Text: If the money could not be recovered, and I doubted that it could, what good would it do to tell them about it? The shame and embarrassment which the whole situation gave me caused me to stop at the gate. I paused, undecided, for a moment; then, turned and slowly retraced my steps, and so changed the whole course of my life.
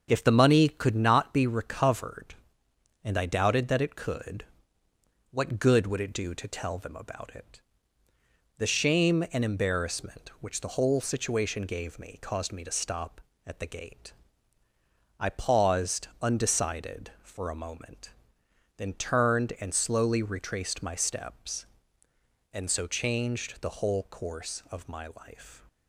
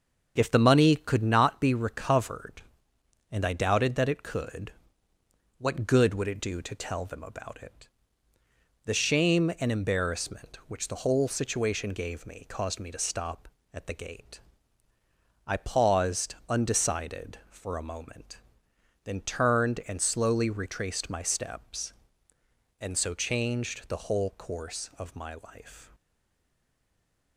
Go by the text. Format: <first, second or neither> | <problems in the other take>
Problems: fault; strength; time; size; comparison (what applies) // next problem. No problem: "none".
first | starts louder than the rest; until 1.3 s; 7 dB; also in the first // stays silent after the last word; noticeable; from 25.9 s on; 1.4 s long